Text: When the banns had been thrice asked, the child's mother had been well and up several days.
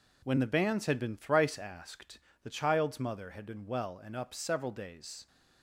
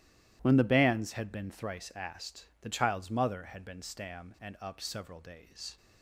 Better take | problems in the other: first | starts louder than the rest; strong; until 1.4 s; 13.5 dB // says "stam" for "well"; at 3.8 s

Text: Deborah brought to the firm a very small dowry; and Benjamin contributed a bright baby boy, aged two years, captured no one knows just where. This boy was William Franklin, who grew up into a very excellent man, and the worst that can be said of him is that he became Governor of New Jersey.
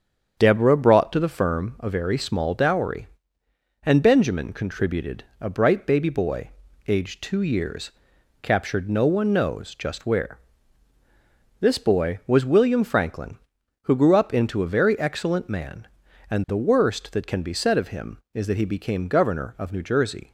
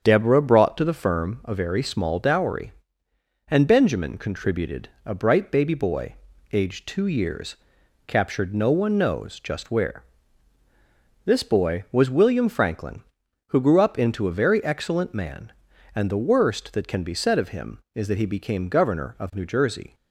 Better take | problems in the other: neither | starts louder than the rest; strong; the same in both // pauses between "contributed" and "a"; slight; the same in both

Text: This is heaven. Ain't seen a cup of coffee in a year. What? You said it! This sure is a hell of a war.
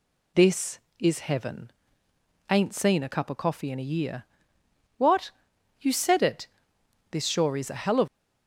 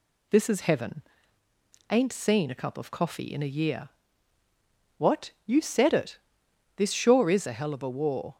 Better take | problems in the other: second | stops before "a war"; at 8.0 s

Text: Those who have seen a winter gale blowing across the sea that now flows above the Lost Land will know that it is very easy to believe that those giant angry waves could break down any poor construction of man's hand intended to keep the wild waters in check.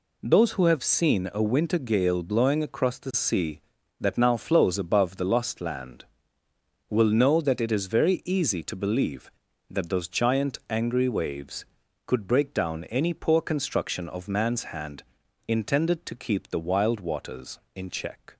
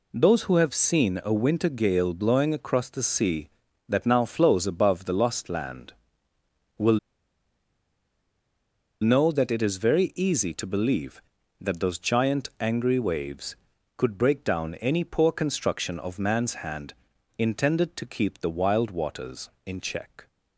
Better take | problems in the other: first | pauses between "will" and "know"; strong; at 6.9 s; 2.0 s long // pauses between "hand" and "intended"; noticeable; at 16.9 s; 0.46 s long; noticeable in the first

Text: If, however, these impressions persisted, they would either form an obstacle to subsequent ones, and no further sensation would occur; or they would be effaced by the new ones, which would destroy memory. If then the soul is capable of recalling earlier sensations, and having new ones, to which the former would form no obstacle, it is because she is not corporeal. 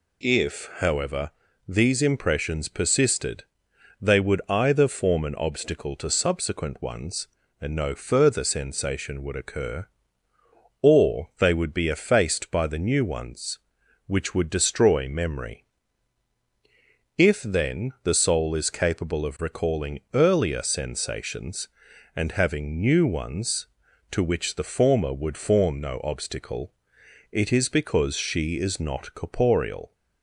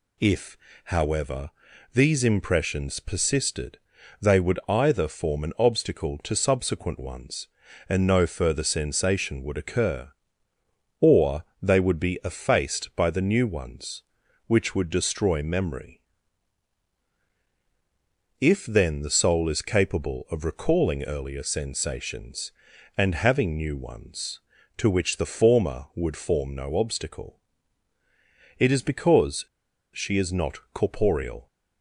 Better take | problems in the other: first | pauses between "or" and "they"; slight; at 11.4 s; 0.18 s long // pauses between "because" and "she"; noticeable; at 29.4 s; 0.49 s long

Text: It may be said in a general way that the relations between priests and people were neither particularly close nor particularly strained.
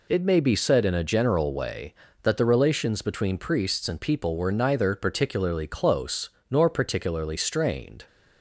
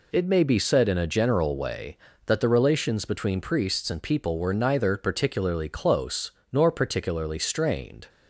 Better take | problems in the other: neither | pauses between "close" and "nor"; slight; the same in both

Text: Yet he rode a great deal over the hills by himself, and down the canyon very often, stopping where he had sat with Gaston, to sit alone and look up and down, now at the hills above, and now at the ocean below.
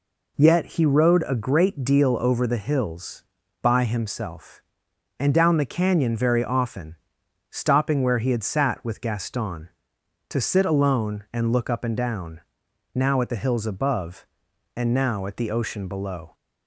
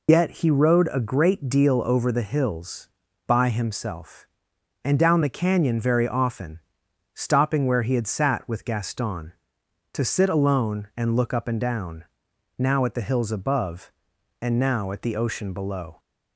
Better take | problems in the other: first | loses the start of "Yet"; at 0.0 s; 85 ms

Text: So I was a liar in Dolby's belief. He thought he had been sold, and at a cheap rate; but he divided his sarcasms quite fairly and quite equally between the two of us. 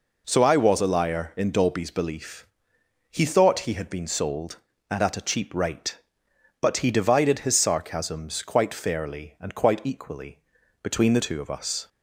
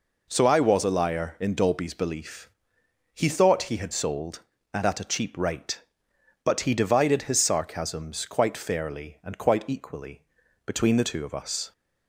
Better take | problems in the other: first | skips "been"; at 3.9 s // pauses between "equally" and "between"; at 10.2 s; 0.42 s long; also in the first

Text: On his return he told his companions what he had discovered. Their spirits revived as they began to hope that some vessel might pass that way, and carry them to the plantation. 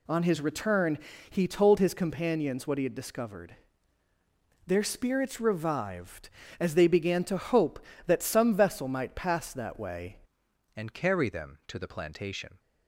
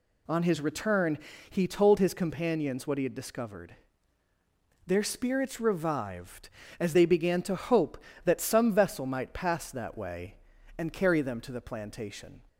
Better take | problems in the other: second | pauses between "return" and "he"; slight; at 0.9 s; 0.32 s long; slight in the second // changes voice at "and"; from 10.7 s on; 1.8 s long

